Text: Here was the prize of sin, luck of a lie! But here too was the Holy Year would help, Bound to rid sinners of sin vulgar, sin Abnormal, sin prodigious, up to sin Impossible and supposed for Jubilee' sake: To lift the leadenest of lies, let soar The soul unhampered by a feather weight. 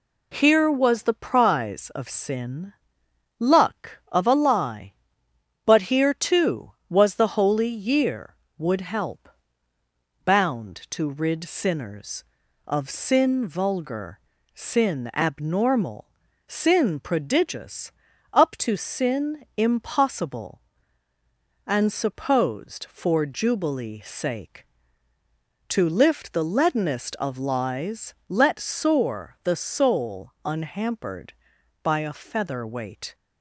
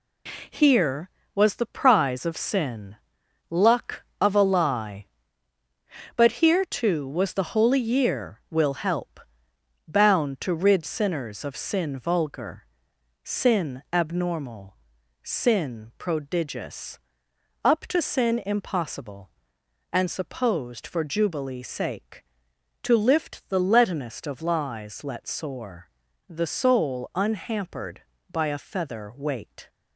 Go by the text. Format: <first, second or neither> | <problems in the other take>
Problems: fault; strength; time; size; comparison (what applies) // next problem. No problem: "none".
first | says "will" for "would"; at 8.5 s // pauses between "soar" and "The"; at 25.8 s; 0.40 s long